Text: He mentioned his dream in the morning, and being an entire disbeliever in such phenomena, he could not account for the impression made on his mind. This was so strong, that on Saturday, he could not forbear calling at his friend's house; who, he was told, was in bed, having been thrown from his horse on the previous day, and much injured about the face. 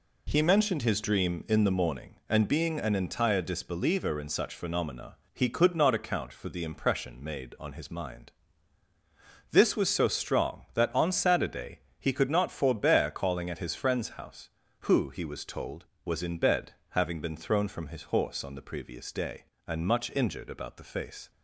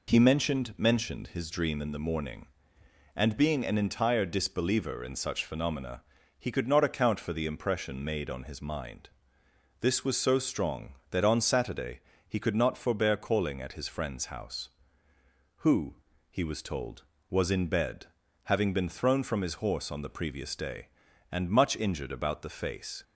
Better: first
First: none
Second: says "mentioned" twice; at 0.7 s

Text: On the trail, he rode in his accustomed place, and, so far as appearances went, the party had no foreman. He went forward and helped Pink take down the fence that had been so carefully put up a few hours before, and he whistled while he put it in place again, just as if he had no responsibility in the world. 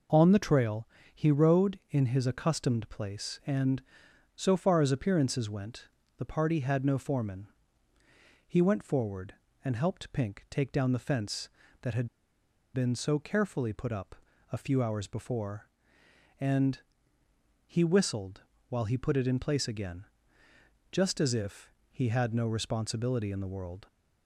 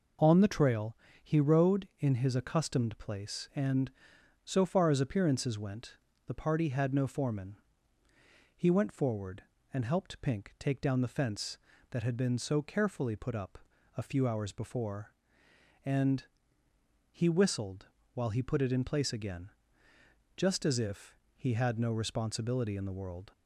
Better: second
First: pauses between "had" and "been"; noticeable; at 12.0 s; 0.66 s long // pauses between "up" and "a"; at 14.1 s; 0.38 s long // pauses between "and" and "he"; noticeable; at 16.7 s; 0.86 s long // pauses between "whistled" and "while"; slight; at 18.4 s; 0.26 s long // pauses between "if" and "he"; slight; at 21.7 s; 0.20 s long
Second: pauses between "up" and "a"; at 13.5 s; 0.40 s long // pauses between "and" and "he"; noticeable; at 16.2 s; 0.86 s long // pauses between "whistled" and "while"; slight; at 17.8 s; 0.26 s long // pauses between "if" and "he"; slight; at 21.1 s; 0.20 s long

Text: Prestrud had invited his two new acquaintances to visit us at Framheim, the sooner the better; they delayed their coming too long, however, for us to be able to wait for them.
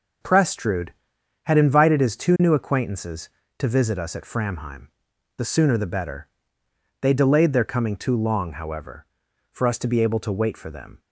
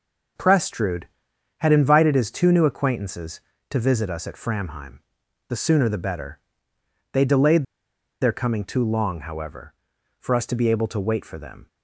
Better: first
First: none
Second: pauses between "delayed" and "their"; noticeable; at 7.6 s; 0.56 s long

